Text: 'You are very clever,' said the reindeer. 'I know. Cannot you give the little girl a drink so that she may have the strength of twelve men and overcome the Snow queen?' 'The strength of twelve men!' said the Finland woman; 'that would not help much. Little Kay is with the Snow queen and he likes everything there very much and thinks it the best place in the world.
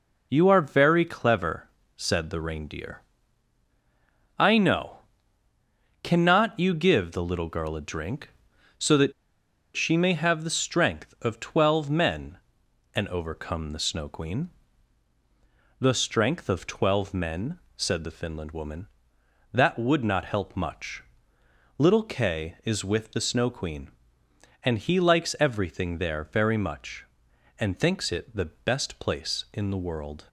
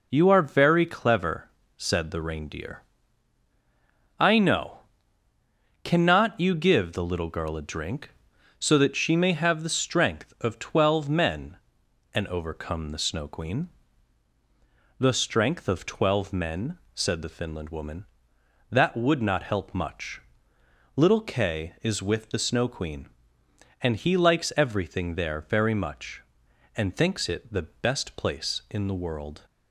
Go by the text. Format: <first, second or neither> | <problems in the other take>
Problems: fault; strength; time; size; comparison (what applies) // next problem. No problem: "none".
second | pauses between "that" and "she"; noticeable; at 9.1 s; 0.64 s long